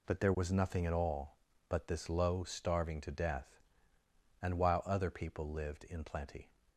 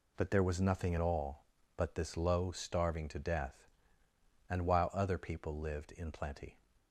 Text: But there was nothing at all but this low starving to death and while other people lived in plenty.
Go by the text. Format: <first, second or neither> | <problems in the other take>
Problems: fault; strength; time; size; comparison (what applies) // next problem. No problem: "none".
neither | none